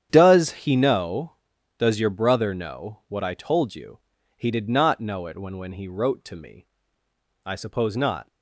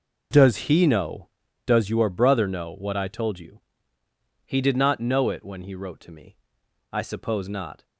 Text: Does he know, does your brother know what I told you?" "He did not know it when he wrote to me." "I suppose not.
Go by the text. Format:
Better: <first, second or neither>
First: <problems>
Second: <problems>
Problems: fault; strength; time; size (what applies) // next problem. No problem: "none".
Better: second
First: starts louder than the rest; strong; until 1.1 s; 9 dB // says "when" twice; at 5.5 s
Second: none